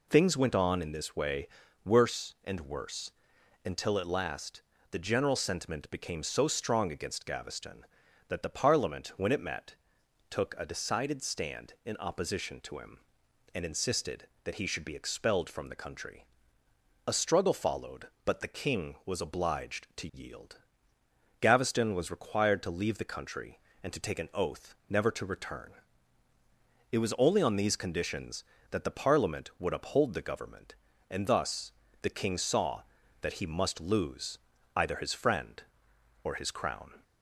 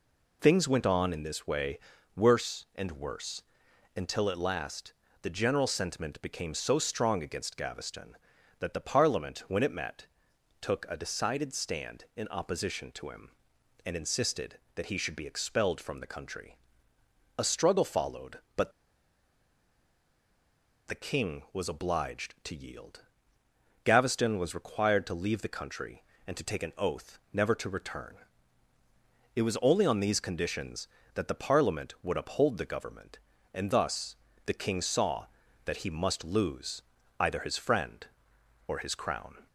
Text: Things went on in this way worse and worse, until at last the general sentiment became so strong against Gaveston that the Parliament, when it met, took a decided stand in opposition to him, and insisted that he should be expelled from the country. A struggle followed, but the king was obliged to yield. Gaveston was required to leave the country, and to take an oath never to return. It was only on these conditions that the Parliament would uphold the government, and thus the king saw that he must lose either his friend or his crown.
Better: first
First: pauses between "way" and "worse"; at 1.4 s; 0.38 s long // pauses between "last" and "the"; slight; at 4.6 s; 0.30 s long // pauses between "thus" and "the"; slight; at 31.7 s; 0.30 s long // pauses between "lose" and "either"; at 34.3 s; 0.38 s long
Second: pauses between "way" and "worse"; at 1.7 s; 0.38 s long // pauses between "last" and "the"; slight; at 4.9 s; 0.30 s long // pauses between "but" and "the"; strong; at 18.7 s; 2.1 s long // pauses between "thus" and "the"; slight; at 34.1 s; 0.30 s long // pauses between "lose" and "either"; at 36.8 s; 0.38 s long

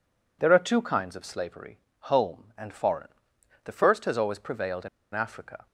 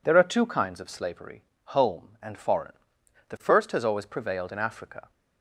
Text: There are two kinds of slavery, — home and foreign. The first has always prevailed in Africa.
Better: second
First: pauses between "in" and "Africa"; slight; at 4.8 s; 0.25 s long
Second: none

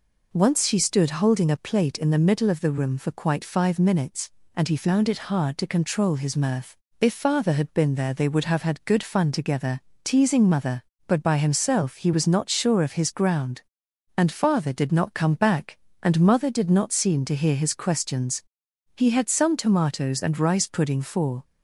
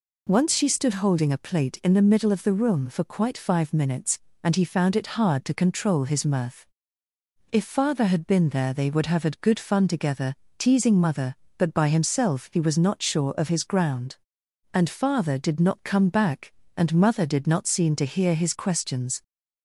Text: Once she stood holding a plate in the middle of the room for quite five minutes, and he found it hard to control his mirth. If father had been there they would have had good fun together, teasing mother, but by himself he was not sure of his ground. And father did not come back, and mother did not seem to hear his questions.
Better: second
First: goes on to say "He had some tomatoes and rice pudding for"; strong; from 18.9 s on; 2.4 s long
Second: none

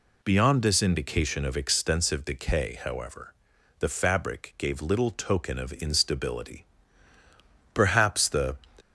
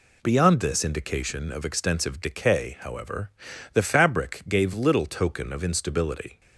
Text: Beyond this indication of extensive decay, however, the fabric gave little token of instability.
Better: second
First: goes on to say "Perhaps the"; noticeable; from 7.7 s on; 0.80 s long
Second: none

